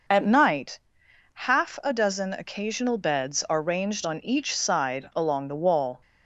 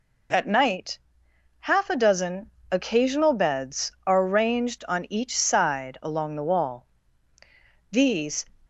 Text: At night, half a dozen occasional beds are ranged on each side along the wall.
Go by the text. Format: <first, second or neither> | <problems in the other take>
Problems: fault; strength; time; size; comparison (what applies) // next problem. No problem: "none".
first | pauses between "dozen" and "occasional"; slight; at 2.5 s; 0.20 s long // goes on to say "These"; from 7.9 s on; 0.56 s long